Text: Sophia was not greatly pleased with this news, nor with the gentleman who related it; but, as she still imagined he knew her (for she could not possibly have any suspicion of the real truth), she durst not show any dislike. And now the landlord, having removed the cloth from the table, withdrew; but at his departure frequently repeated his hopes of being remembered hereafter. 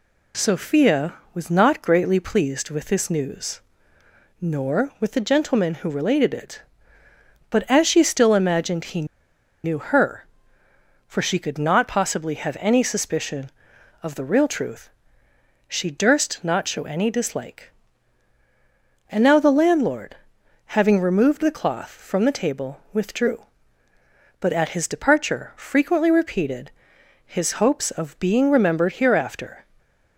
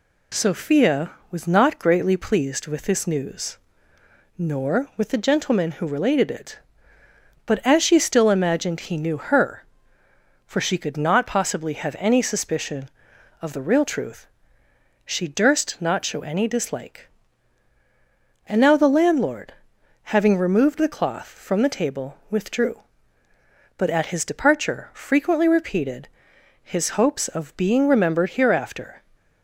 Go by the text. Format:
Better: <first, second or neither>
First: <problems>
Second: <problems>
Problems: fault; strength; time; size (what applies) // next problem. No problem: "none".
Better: second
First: pauses between "he" and "knew"; noticeable; at 9.0 s; 0.57 s long // pauses between "repeated" and "his"; noticeable; at 26.6 s; 0.56 s long // stays silent after the last word; slight; from 29.6 s on; 0.5 s long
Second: pauses between "repeated" and "his"; noticeable; at 26.0 s; 0.56 s long